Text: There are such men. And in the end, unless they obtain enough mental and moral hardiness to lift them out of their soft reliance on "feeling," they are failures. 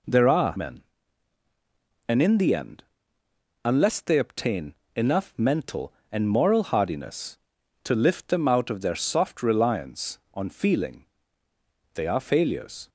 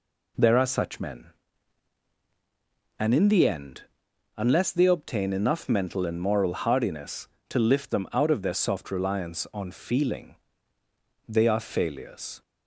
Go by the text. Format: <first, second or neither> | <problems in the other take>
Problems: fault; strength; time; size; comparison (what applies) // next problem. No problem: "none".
second | skips "such"; at 0.5 s // pauses between "obtain" and "enough"; slight; at 4.7 s; 0.24 s long